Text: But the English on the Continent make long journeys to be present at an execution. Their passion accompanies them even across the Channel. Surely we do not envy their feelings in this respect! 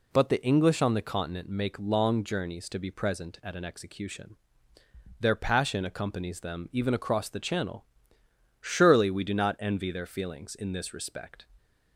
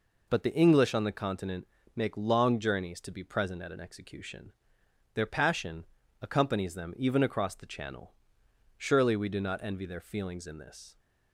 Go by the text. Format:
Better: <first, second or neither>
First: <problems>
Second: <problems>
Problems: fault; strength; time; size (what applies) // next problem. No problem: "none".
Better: first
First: none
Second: pauses between "Continent" and "make"; slight; at 1.6 s; 0.28 s long // pauses between "passion" and "accompanies"; slight; at 5.8 s; 0.36 s long // stops before "respect"; at 10.9 s